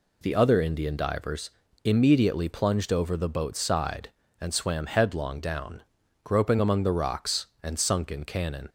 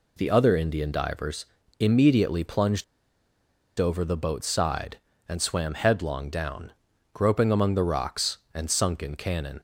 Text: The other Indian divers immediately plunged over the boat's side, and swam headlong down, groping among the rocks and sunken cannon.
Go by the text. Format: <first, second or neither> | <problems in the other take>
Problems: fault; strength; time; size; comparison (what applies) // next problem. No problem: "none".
first | pauses between "divers" and "immediately"; slight; at 1.4 s; 0.34 s long; slight in the first // pauses between "plunged" and "over"; noticeable; at 2.8 s; 0.95 s long